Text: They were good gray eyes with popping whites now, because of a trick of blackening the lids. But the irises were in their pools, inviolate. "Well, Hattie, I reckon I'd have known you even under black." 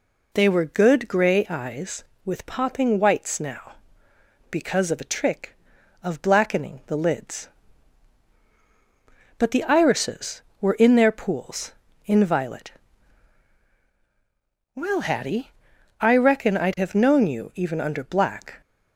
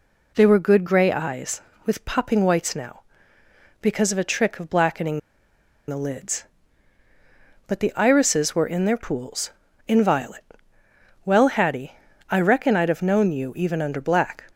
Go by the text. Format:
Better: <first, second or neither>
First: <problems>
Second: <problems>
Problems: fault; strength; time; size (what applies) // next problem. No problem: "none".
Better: first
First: none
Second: pauses between "blackening" and "the"; noticeable; at 5.1 s; 0.69 s long